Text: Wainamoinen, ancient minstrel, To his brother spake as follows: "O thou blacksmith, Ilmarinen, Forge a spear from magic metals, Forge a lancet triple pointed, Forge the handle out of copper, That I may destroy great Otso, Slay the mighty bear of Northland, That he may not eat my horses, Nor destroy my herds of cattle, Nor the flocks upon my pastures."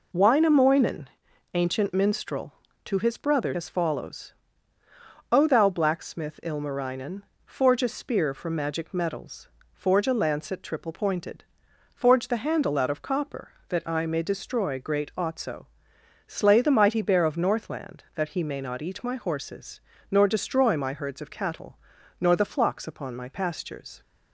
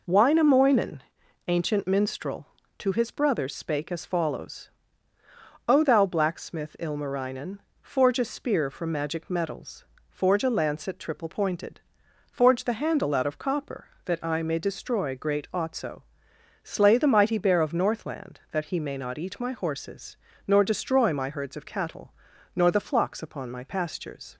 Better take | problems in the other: second | skips "spake"; at 3.5 s

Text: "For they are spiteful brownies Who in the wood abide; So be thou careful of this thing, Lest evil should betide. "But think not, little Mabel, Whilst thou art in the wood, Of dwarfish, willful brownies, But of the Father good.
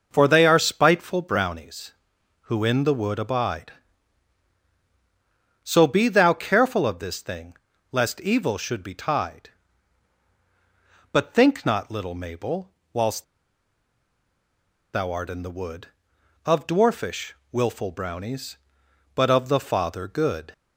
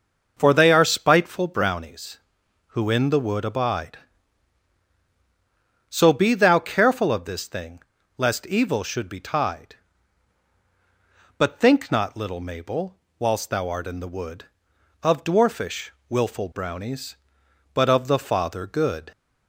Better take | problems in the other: second | pauses between "Whilst" and "thou"; strong; at 13.2 s; 1.6 s long

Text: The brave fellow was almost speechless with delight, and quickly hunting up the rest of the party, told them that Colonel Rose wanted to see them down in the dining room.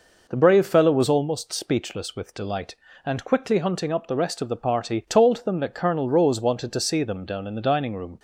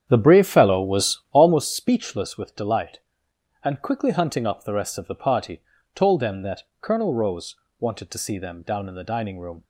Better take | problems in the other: first | starts louder than the rest; strong; until 1.7 s; 8.5 dB // pauses between "that" and "Colonel"; slight; at 6.6 s; 0.16 s long // pauses between "Rose" and "wanted"; slight; at 7.5 s; 0.24 s long

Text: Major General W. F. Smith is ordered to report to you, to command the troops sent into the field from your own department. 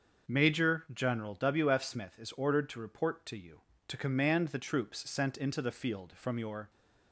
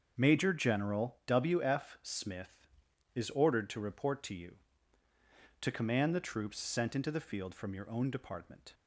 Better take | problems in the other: second | starts louder than the rest; until 1.3 s; 6 dB; also in the second // stops before "own department"; at 6.6 s

